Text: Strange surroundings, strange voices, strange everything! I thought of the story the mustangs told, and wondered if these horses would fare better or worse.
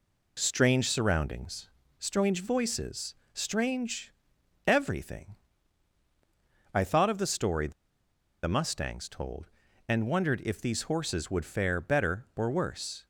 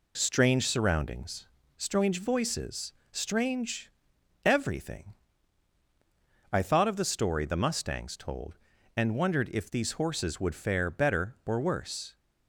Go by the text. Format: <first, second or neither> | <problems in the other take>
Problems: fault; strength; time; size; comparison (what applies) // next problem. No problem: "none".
second | pauses between "strange" and "everything"; noticeable; at 4.1 s; 0.56 s long; noticeable in the second // pauses between "the" and "mustangs"; noticeable; at 7.7 s; 0.73 s long